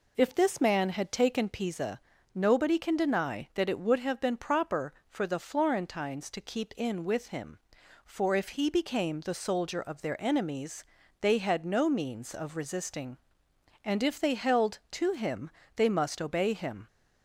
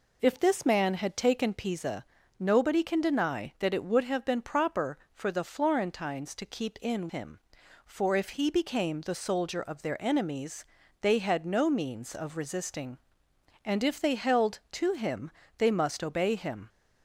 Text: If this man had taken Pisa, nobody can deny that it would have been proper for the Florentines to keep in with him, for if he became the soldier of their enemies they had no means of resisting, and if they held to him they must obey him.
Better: first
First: pauses between "enemies" and "they"; slight; at 10.8 s; 0.36 s long // pauses between "him" and "they"; slight; at 15.4 s; 0.24 s long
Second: skips "with"; at 7.0 s // pauses between "enemies" and "they"; slight; at 10.6 s; 0.36 s long // pauses between "him" and "they"; slight; at 15.3 s; 0.26 s long

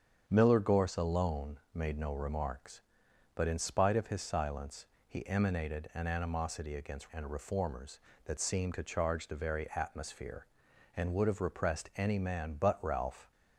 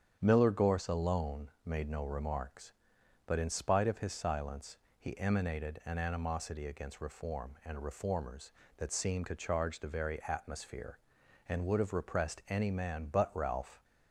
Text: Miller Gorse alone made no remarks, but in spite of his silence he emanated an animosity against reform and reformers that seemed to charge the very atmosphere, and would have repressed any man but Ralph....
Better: second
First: starts louder than the rest; strong; until 1.2 s; 7.5 dB // pauses between "silence" and "he"; slight; at 4.8 s; 0.22 s long // skips "reform"; at 7.0 s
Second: starts louder than the rest; strong; until 1.2 s; 8.5 dB // pauses between "silence" and "he"; slight; at 4.7 s; 0.22 s long

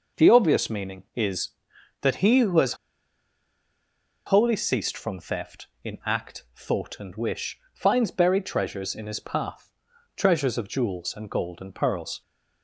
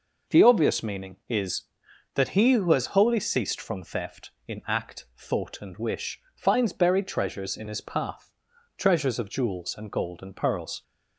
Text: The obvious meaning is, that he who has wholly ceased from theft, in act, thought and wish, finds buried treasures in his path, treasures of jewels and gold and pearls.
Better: second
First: pauses between "has" and "wholly"; strong; at 2.7 s; 1.5 s long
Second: none

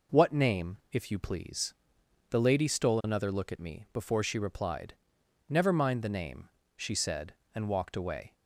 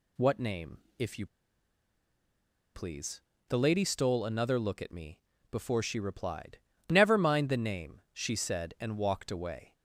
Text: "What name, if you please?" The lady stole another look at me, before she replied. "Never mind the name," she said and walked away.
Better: first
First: none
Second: pauses between "you" and "please"; strong; at 1.2 s; 1.4 s long

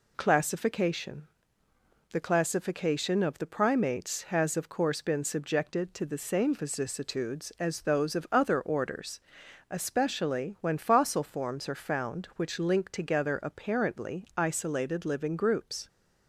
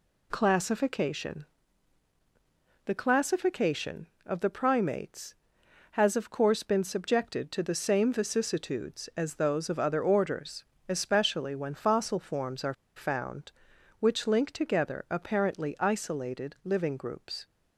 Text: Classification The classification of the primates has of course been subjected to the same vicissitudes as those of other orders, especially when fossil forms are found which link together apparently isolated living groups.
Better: first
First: pauses between "Classification" and "The"; noticeable; at 1.2 s; 0.88 s long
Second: pauses between "Classification" and "The"; strong; at 1.4 s; 1.4 s long // pauses between "are" and "found"; slight; at 12.7 s; 0.22 s long

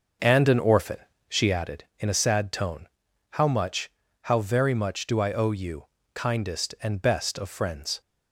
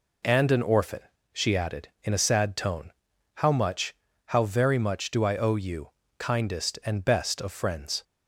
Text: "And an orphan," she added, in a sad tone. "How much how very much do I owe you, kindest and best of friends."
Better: second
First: starts louder than the rest; until 1.6 s; 6.5 dB // pauses between "much" and "how"; slight; at 3.8 s; 0.34 s long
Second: pauses between "much" and "how"; slight; at 3.9 s; 0.34 s long

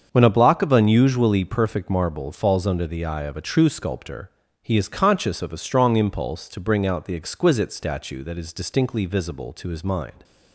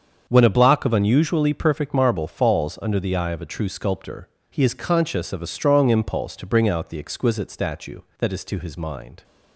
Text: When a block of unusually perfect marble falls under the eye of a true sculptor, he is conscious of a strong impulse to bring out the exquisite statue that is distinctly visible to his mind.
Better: first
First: starts louder than the rest; until 1.1 s; 7 dB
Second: starts louder than the rest; until 1.2 s; 7 dB // skips "distinctly visible"; at 8.4 s

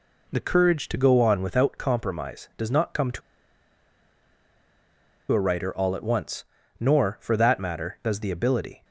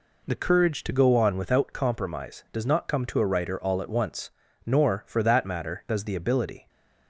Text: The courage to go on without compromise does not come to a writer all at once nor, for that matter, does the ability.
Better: second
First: pauses between "to" and "a"; strong; at 3.2 s; 2.1 s long // pauses between "once" and "nor"; slight; at 6.4 s; 0.34 s long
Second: pauses between "once" and "nor"; slight; at 4.3 s; 0.34 s long

